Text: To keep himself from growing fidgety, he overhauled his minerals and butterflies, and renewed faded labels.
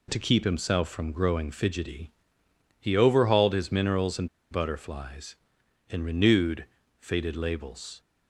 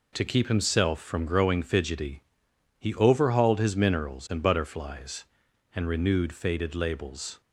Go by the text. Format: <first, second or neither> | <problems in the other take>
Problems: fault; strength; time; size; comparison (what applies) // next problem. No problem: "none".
second | pauses between "and" and "butterflies"; slight; at 4.2 s; 0.23 s long // pauses between "renewed" and "faded"; slight; at 6.6 s; 0.36 s long